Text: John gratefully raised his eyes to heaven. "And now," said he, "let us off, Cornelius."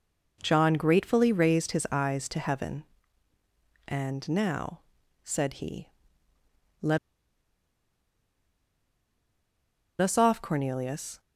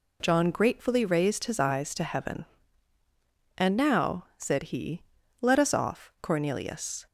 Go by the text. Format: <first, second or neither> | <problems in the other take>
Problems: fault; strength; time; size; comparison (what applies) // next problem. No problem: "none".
second | pauses between "let" and "us"; strong; at 6.9 s; 3.0 s long